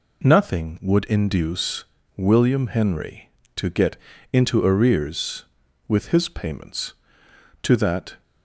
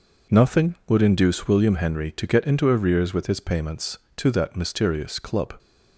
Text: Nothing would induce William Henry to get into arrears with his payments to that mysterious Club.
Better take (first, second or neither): second